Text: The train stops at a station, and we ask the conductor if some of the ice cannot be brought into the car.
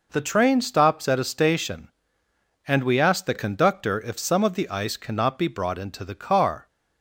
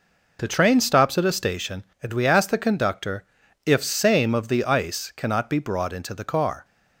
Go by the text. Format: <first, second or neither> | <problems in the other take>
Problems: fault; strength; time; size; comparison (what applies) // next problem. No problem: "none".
first | pauses between "conductor" and "if"; at 3.2 s; 0.42 s long // says "same" for "some"; at 3.8 s